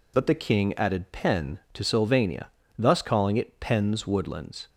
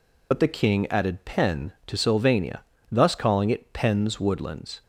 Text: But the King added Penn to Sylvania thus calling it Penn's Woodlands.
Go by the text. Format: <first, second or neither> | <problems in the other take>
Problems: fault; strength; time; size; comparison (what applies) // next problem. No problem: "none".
first | loses the start of "But"; at 0.3 s; 40 ms // pauses between "Sylvania" and "thus"; slight; at 2.6 s; 0.30 s long; slight in the first